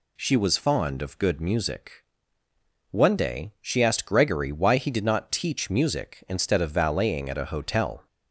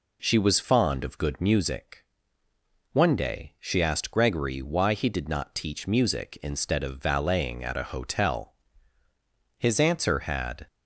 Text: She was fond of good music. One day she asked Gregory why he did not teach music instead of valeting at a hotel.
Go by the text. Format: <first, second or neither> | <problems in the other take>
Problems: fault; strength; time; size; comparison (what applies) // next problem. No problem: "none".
first | goes on to say "His answer had"; noticeable; from 9.5 s on; 1.1 s long